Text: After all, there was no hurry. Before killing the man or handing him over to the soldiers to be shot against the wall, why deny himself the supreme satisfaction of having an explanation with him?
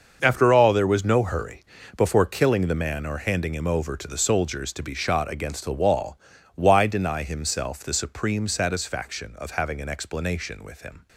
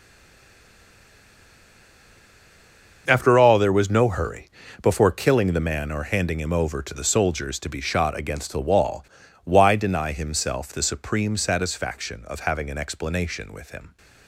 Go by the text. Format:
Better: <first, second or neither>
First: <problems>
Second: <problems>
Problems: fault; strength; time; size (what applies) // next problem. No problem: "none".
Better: first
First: starts louder than the rest; until 1.2 s; 6.5 dB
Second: stays silent before the first word; strong; until 3.0 s; 3.0 s long // starts louder than the rest; until 4.0 s; 6.5 dB